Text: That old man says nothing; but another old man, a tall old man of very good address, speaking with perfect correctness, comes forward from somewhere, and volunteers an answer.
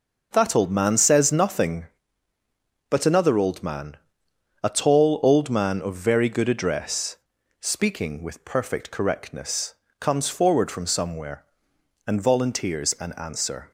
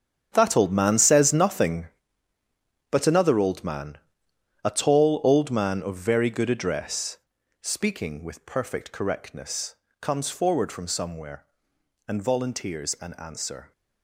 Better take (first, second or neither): first